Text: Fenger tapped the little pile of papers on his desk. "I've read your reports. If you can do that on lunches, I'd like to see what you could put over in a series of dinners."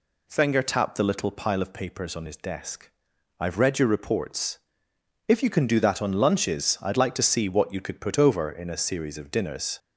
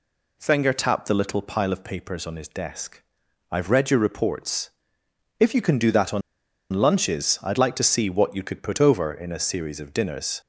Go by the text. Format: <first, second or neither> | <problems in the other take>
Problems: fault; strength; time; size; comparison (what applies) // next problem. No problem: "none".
first | pauses between "on" and "lunches"; noticeable; at 6.2 s; 0.51 s long